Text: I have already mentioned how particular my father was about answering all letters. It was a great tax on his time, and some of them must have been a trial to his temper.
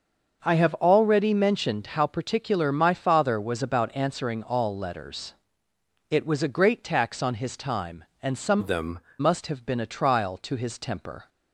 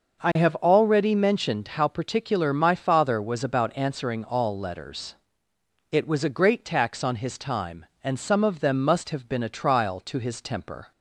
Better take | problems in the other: second | starts louder than the rest; until 1.4 s; 6.5 dB // changes voice from "of" to "them"; from 8.5 to 8.9 s; 0.4 s long

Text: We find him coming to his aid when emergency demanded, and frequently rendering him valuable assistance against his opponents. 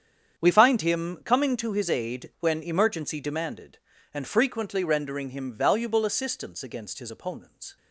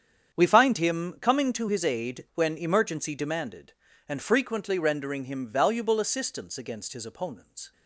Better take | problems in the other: neither | starts louder than the rest; strong; the same in both

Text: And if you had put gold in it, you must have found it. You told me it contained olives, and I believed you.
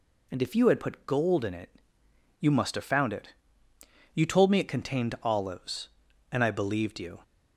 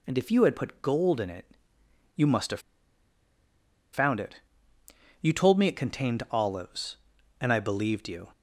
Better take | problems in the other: first | pauses between "have" and "found"; strong; at 2.6 s; 1.3 s long

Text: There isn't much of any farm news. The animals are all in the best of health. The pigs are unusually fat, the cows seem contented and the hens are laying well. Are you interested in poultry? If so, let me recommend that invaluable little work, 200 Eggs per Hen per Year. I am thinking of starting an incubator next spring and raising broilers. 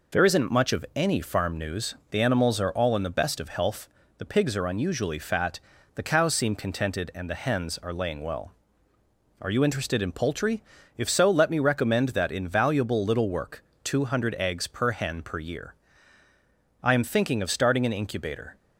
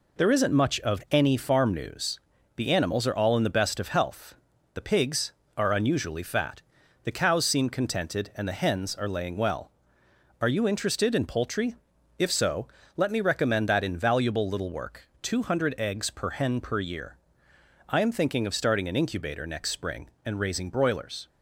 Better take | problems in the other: second | stops before "next spring and raising broilers"; at 18.5 s

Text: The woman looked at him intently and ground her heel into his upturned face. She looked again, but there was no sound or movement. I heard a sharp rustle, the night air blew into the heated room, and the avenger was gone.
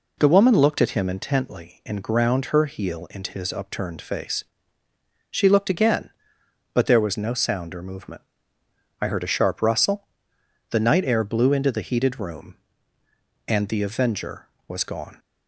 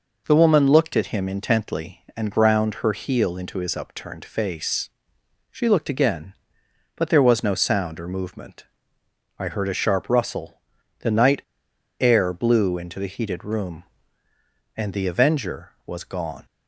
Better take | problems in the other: first | pauses between "night" and "air"; noticeable; at 11.4 s; 0.57 s long

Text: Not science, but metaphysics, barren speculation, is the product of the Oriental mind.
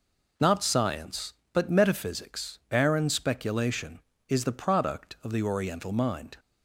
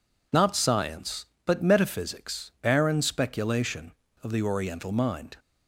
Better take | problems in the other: first | skips "is the product"; at 4.0 s

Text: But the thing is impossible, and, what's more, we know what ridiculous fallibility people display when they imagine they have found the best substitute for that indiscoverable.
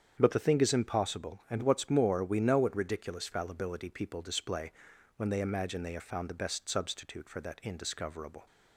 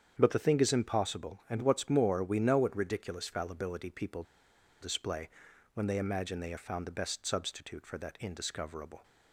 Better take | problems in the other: first | starts louder than the rest; strong; until 1.1 s; 8 dB; strong in the first // pauses between "people" and "display"; noticeable; at 4.2 s; 0.58 s long // pauses between "display" and "when"; at 5.2 s; 0.44 s long; also in the first

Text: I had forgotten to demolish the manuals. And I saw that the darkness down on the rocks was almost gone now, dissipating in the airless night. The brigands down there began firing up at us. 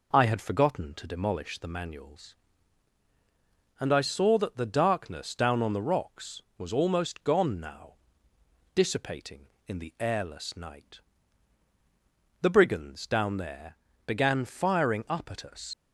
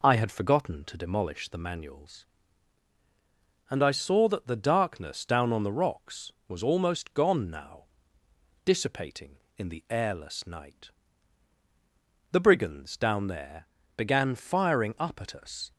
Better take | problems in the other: second | pauses between "there" and "began"; slight; at 13.7 s; 0.30 s long; slight in the second // leaves "us" unfinished; at 15.7 s; 80 ms

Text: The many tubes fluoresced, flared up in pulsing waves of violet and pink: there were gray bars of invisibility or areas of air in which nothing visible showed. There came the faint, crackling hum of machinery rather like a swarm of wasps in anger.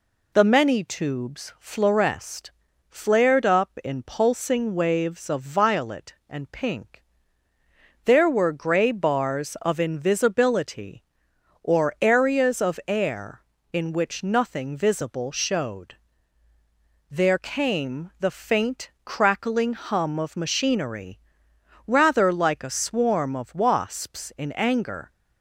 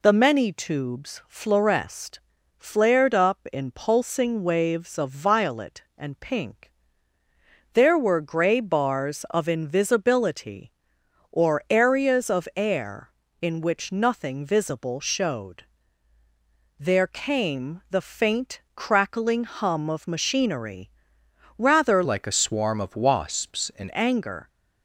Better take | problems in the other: first | pauses between "machinery" and "rather"; noticeable; at 20.8 s; 0.70 s long; noticeable in the first // changes voice from "like" to "in"; from 22.0 to 23.8 s; 1.8 s long

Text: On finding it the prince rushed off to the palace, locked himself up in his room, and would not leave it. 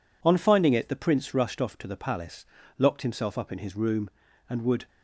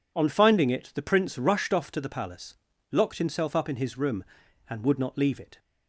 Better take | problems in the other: second | stops before "not leave it"; at 4.8 s

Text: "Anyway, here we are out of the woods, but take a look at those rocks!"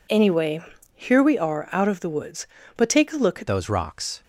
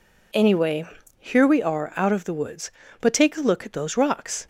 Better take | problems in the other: second | changes voice at "those"; from 3.4 s on; 0.8 s long

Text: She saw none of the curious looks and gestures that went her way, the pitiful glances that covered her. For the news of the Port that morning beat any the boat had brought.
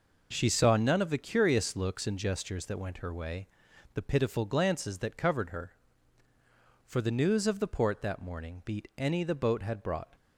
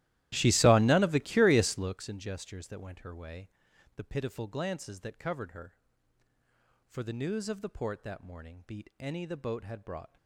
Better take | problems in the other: first | starts louder than the rest; strong; until 2.0 s; 15 dB

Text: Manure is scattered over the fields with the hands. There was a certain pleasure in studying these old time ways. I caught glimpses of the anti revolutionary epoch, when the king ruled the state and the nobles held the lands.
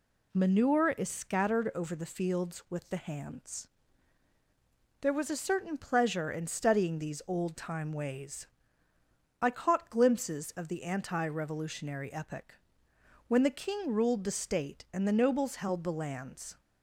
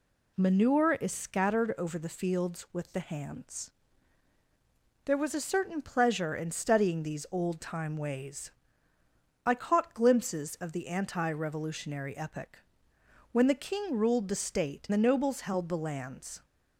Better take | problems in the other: first | skips "and"; at 14.9 s

